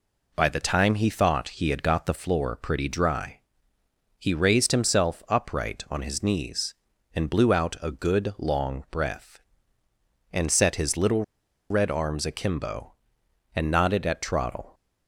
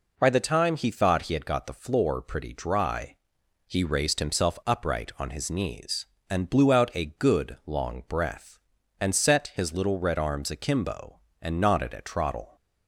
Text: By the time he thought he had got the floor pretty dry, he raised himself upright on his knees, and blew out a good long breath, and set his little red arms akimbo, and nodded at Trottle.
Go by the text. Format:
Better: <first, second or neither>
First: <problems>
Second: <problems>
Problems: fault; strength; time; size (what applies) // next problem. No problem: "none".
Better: second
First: pauses between "little" and "red"; at 11.2 s; 0.45 s long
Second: none